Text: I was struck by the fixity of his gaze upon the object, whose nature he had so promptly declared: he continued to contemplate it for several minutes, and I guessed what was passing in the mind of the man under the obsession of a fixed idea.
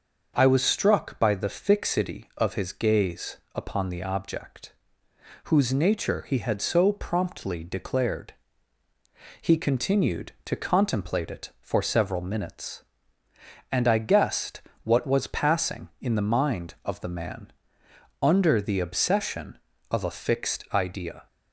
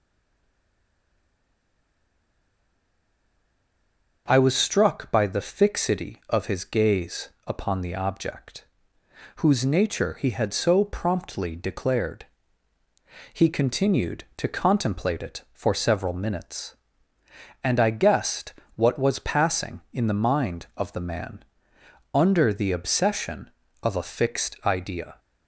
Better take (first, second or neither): first